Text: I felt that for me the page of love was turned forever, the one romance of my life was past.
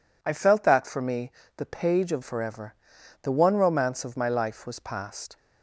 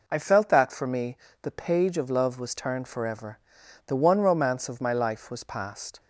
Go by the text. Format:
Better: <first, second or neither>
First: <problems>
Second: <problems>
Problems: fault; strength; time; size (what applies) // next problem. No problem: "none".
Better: second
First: pauses between "me" and "the"; slight; at 1.3 s; 0.26 s long // skips "love was turned"; at 2.2 s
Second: pauses between "me" and "the"; slight; at 1.1 s; 0.26 s long